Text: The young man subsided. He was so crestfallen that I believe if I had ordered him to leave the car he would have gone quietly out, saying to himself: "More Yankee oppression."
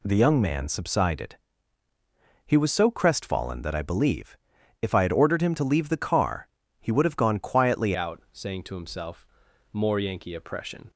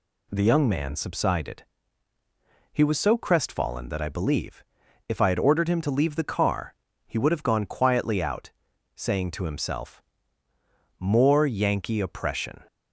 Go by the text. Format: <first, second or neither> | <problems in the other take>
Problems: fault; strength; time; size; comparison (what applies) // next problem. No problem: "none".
second | pauses between "believe" and "if"; at 4.3 s; 0.44 s long; also in the second // pauses between "car" and "he"; slight; at 6.4 s; 0.32 s long; slight in the second // changes voice at "out"; from 7.9 s on; 2.9 s long